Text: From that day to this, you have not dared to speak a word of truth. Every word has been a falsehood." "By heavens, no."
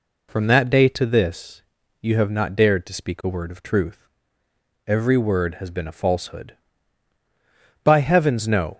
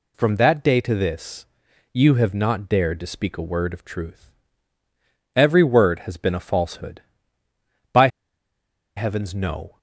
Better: first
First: none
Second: pauses between "By" and "heavens"; noticeable; at 8.0 s; 0.89 s long

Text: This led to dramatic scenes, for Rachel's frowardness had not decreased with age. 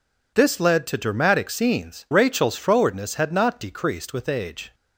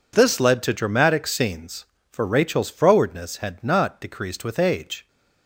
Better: second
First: skips "for"; at 2.0 s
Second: none

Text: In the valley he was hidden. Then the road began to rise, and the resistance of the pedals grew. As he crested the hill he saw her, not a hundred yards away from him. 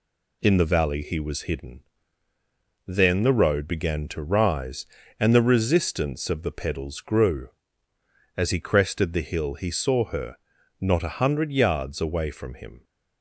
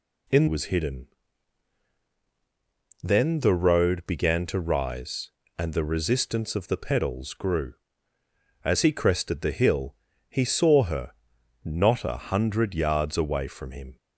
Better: first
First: none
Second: skips "the valley he"; at 0.4 s // pauses between "hill" and "he"; slight; at 9.9 s; 0.34 s long

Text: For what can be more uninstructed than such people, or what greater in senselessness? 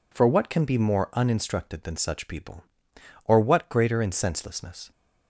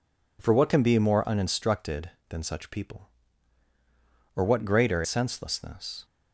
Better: first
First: none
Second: skips "in"; at 5.0 s

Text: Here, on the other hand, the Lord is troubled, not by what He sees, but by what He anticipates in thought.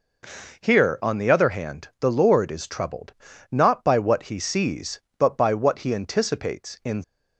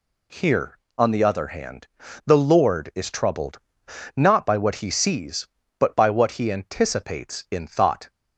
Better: second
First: stops before "thought"; at 7.0 s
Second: none

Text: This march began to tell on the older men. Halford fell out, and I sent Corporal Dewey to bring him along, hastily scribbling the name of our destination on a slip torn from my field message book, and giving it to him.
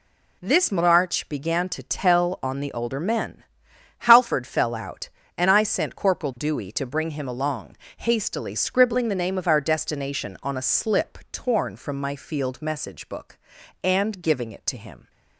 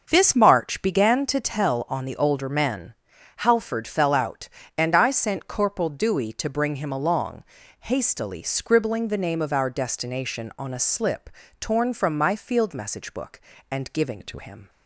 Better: first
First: none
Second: starts louder than the rest; until 1.1 s; 6.5 dB // pauses between "slip" and "torn"; slight; at 11.2 s; 0.32 s long // changes voice from "it" to "to"; from 14.1 to 14.3 s; 0.2 s long

